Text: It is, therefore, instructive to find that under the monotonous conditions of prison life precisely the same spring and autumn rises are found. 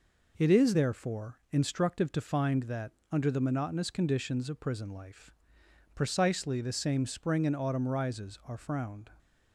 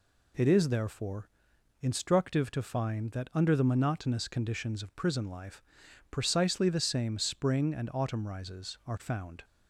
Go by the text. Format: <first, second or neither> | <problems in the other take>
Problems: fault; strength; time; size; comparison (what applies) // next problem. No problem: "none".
second | pauses between "that" and "under"; slight; at 2.8 s; 0.22 s long // pauses between "life" and "precisely"; noticeable; at 5.3 s; 0.62 s long; noticeable in the second // says "frowned" for "found"; at 8.5 s